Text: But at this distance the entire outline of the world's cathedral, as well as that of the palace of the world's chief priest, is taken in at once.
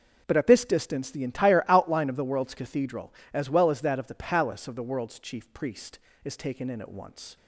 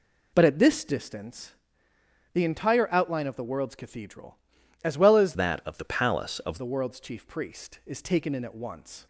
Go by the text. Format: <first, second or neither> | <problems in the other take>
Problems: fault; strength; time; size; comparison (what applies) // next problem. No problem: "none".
first | pauses between "distance" and "the"; noticeable; at 1.5 s; 0.80 s long // changes voice from "that" to "of"; from 5.3 to 6.5 s; 1.2 s long